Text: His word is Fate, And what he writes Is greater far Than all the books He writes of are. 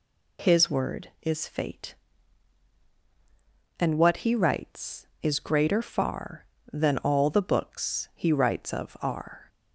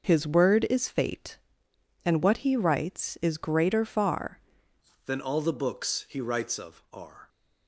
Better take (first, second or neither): first